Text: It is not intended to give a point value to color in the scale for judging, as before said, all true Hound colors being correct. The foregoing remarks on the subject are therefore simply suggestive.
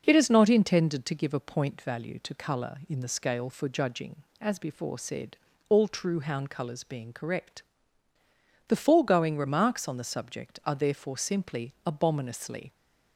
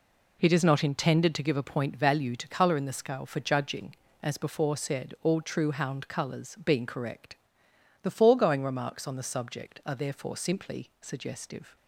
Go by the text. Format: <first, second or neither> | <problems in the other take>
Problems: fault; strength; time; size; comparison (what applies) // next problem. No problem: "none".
second | says "abominously" for "suggestive"; at 11.8 s